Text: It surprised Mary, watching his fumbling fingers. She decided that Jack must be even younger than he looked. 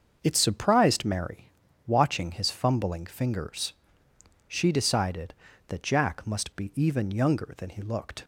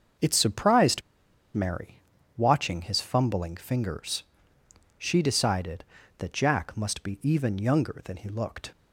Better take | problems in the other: first | starts louder than the rest; until 1.7 s; 6.5 dB; also in the first // pauses between "surprised" and "Mary"; noticeable; at 1.0 s; 0.54 s long

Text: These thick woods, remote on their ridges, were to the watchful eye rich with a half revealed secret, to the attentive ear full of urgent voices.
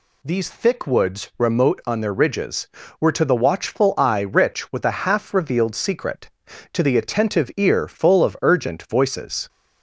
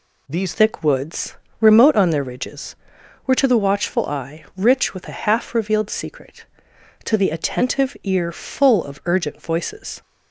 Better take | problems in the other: first | changes voice at "thick"; from 0.5 s on; 9.5 s long

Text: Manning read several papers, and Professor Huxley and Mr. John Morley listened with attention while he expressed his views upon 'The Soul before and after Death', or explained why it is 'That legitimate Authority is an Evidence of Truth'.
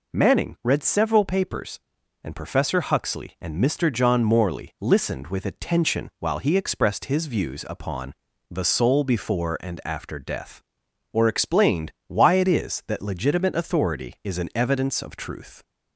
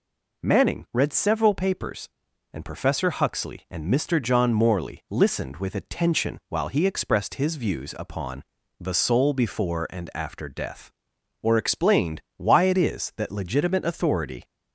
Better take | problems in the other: first | pauses between "upon" and "The"; slight; at 8.4 s; 0.36 s long; slight in the first // stops before "is an Evidence of Truth"; at 14.4 s

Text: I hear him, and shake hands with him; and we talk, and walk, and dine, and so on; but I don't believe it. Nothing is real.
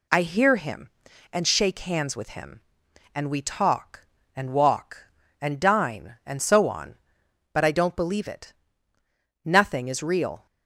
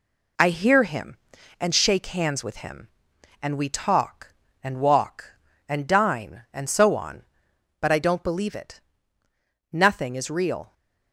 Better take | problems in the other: first | gets quieter; noticeable; throughout; 4 dB

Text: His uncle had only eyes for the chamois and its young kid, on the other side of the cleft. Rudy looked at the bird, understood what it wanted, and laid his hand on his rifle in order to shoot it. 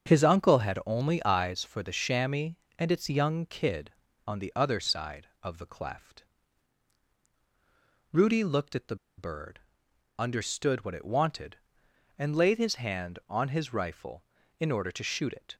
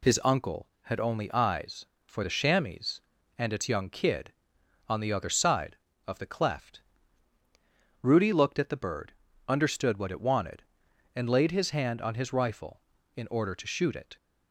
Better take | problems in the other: second | starts louder than the rest; strong; until 1.1 s; 7 dB // pauses between "the" and "bird"; slight; at 8.9 s; 0.22 s long

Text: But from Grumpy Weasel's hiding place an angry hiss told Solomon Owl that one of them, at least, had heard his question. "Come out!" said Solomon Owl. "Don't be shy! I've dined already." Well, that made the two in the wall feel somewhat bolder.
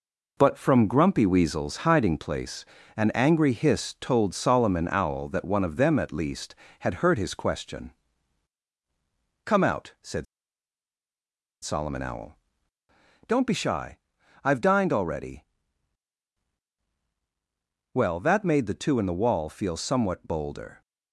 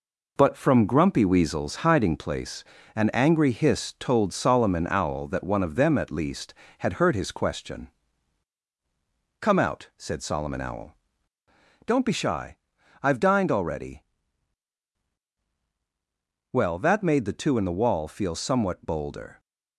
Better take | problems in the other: second | pauses between "place" and "an"; slight; at 2.6 s; 0.32 s long; slight in the second // pauses between "said" and "Solomon"; strong; at 10.2 s; 1.3 s long

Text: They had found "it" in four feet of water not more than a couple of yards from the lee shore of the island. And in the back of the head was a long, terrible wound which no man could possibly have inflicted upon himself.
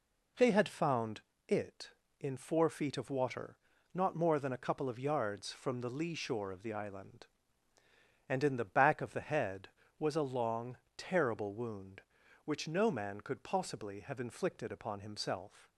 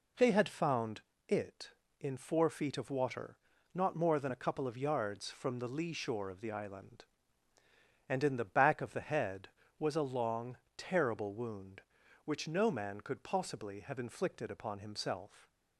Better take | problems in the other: neither | pauses between "found" and "it"; slight; the same in both // pauses between "water" and "not"; slight; the same in both

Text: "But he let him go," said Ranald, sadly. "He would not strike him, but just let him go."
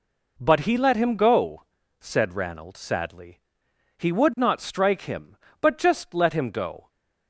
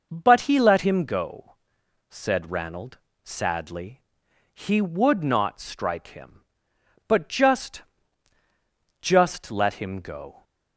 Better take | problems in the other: first | says "just" twice; at 8.9 s

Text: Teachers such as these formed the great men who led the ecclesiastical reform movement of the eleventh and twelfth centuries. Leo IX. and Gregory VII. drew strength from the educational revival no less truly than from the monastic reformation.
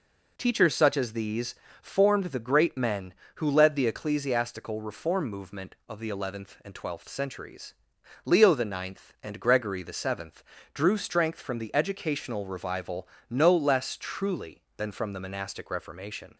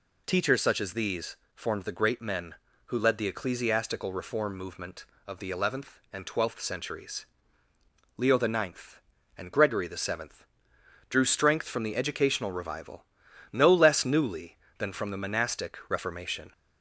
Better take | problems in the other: first | pauses between "these" and "formed"; slight; at 1.3 s; 0.18 s long; slight in the first // pauses between "revival" and "no"; noticeable; at 13.0 s; 0.48 s long; slight in the first // says "newly" for "truly"; at 14.0 s

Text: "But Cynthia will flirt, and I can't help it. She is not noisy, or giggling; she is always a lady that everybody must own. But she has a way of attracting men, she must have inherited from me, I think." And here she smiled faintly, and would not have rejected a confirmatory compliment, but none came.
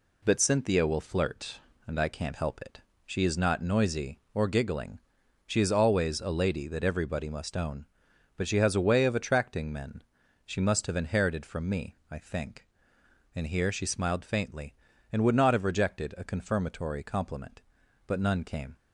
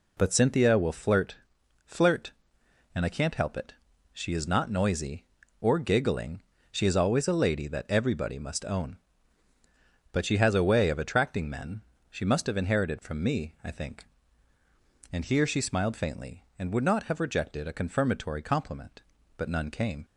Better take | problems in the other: first | says "flirt" twice; at 1.8 s

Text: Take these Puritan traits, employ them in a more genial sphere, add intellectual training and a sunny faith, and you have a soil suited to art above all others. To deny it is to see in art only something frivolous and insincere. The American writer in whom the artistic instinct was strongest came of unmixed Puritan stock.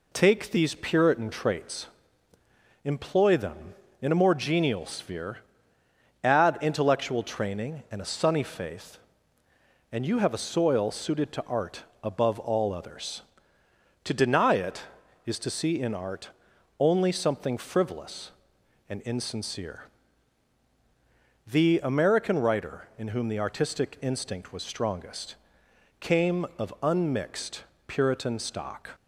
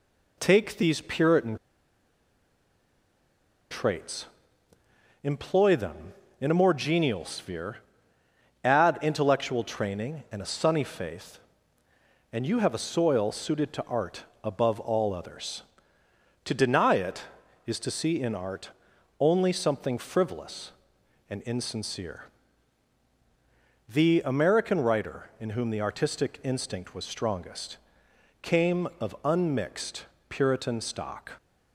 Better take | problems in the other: first | pauses between "Puritan" and "traits"; strong; at 1.5 s; 2.1 s long // pauses between "art" and "above"; slight; at 14.2 s; 0.20 s long; slight in the first // pauses between "art" and "only"; noticeable; at 18.6 s; 0.50 s long; noticeable in the first // pauses between "strongest" and "came"; noticeable; at 27.7 s; 0.64 s long; noticeable in the first // pauses between "unmixed" and "Puritan"; slight; at 30.0 s; 0.24 s long; slight in the first

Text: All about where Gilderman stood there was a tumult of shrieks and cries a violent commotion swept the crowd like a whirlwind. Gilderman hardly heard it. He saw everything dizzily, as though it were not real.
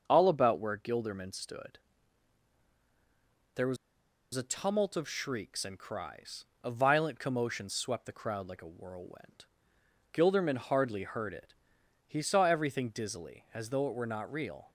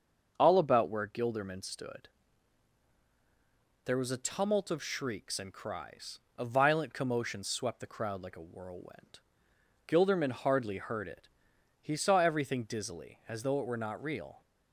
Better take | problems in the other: second | starts louder than the rest; until 1.0 s; 6.5 dB; also in the second // pauses between "stood" and "there"; strong; at 1.7 s; 1.7 s long; strong in the second // pauses between "was" and "a"; noticeable; at 3.7 s; 0.58 s long // pauses between "cries" and "a"; slight; at 6.4 s; 0.20 s long; slight in the second

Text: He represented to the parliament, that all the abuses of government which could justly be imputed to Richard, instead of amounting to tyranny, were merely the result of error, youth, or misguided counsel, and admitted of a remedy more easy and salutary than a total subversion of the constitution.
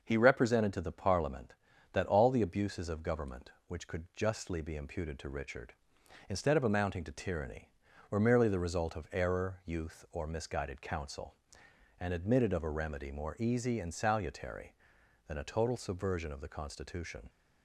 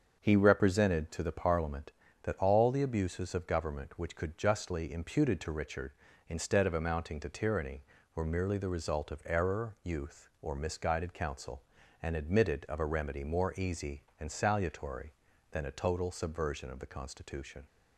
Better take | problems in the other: first | starts louder than the rest; until 1.2 s; 7 dB // skips "be"; at 4.9 s

